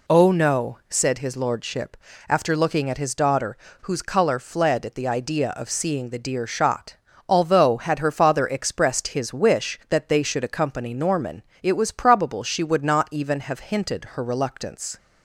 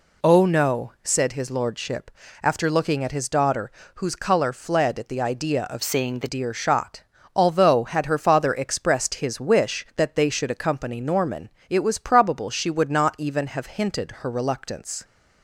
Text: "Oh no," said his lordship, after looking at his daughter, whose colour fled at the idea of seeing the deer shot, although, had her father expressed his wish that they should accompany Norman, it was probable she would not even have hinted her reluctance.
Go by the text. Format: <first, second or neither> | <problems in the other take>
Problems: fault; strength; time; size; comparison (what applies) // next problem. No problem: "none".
first | changes voice from "seeing" to "the"; from 5.8 to 6.2 s; 0.4 s long